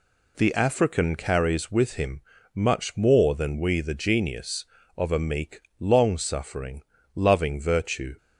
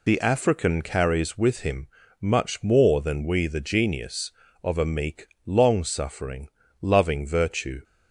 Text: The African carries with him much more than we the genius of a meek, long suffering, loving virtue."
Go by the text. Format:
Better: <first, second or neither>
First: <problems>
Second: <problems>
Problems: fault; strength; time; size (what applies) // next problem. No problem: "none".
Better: first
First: pauses between "him" and "much"; slight; at 2.2 s; 0.32 s long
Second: loses the start of "The"; at 0.0 s; 35 ms // pauses between "him" and "much"; slight; at 1.8 s; 0.32 s long